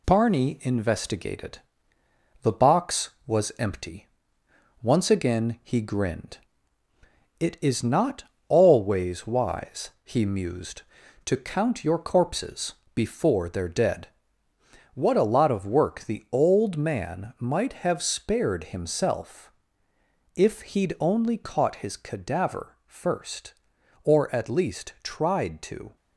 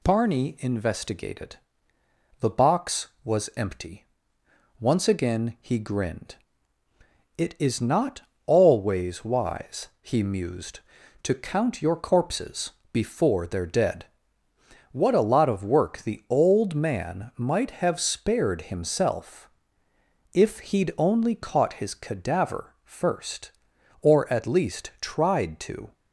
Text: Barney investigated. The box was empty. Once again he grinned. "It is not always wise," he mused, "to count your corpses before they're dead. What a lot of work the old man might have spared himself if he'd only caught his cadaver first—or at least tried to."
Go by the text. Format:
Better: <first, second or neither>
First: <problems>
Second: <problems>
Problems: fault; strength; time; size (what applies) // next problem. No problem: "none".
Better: second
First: gets quieter; throughout; 4 dB // pauses between "not" and "always"; slight; at 8.2 s; 0.22 s long // pauses between "corpses" and "before"; slight; at 12.7 s; 0.20 s long // pauses between "himself" and "if"; noticeable; at 19.5 s; 0.84 s long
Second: pauses between "not" and "always"; slight; at 8.2 s; 0.22 s long // pauses between "corpses" and "before"; slight; at 12.7 s; 0.20 s long // pauses between "himself" and "if"; noticeable; at 19.4 s; 0.84 s long